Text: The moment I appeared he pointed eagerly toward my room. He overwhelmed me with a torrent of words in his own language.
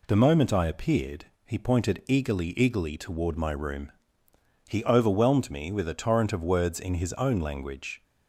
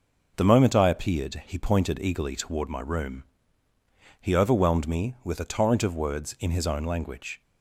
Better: second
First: pauses between "appeared" and "he"; slight; at 1.2 s; 0.22 s long // says "eagerly" twice; at 2.5 s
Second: none

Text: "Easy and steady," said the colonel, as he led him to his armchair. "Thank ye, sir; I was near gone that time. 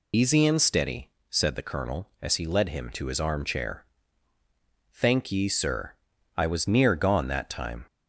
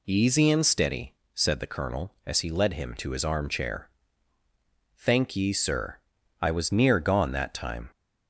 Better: second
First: loses the start of "Easy"; at 0.1 s; 115 ms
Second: none

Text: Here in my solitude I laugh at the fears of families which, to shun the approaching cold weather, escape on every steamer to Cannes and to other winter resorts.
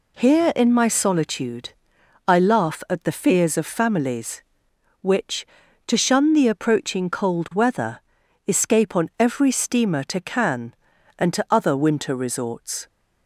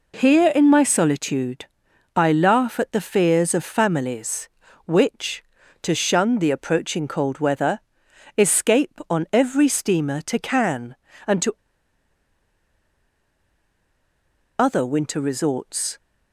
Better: first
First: pauses between "solitude" and "I"; noticeable; at 1.7 s; 0.54 s long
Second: pauses between "solitude" and "I"; noticeable; at 1.6 s; 0.50 s long // pauses between "to" and "other"; strong; at 11.5 s; 3.0 s long

